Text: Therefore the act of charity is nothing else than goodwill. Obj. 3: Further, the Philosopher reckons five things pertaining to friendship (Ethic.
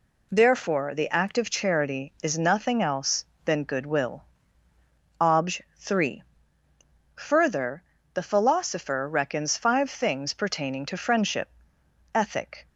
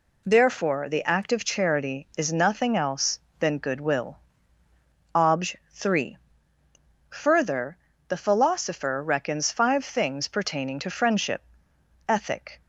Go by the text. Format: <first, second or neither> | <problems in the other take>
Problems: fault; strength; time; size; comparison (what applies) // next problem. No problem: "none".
neither | none